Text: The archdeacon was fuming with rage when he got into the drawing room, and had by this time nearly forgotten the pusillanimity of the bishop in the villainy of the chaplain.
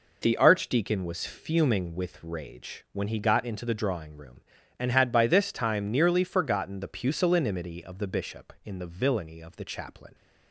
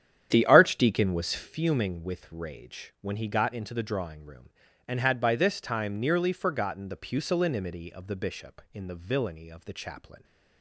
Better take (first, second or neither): first